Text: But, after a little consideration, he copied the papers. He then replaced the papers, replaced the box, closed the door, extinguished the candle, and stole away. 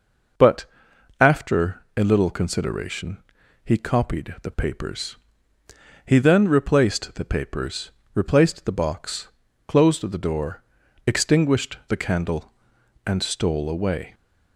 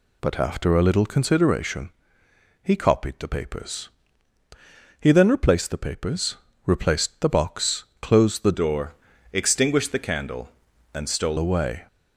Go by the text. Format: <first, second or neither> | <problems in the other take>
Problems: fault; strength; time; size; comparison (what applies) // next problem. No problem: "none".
first | changes voice from "door" to "stole"; from 8.5 to 11.3 s; 2.8 s long